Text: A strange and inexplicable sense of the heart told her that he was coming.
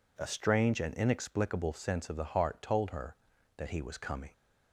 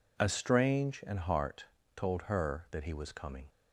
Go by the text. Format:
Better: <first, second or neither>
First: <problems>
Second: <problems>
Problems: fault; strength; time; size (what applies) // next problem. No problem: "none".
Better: first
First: none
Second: skips "inexplicable sense of the"; at 1.1 s // pauses between "heart" and "told"; slight; at 1.6 s; 0.30 s long